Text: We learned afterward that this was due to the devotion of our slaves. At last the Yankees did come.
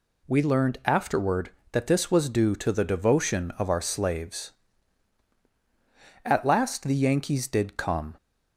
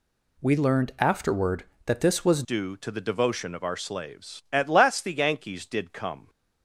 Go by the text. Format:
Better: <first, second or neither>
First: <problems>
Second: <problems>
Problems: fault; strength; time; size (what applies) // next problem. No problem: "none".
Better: first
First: none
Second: changes voice at "due"; from 2.4 s on; 3.8 s long